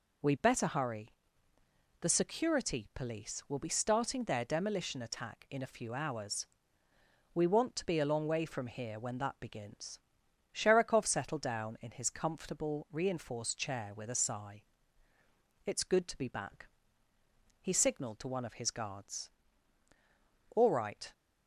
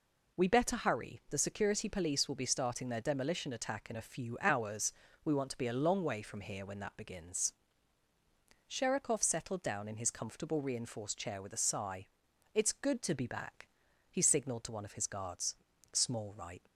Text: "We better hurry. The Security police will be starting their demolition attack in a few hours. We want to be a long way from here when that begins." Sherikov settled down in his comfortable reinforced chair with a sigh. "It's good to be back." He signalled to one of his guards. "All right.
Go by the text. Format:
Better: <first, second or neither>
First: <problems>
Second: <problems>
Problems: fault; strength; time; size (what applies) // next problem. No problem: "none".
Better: first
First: none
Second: says "Small" for "All"; at 15.9 s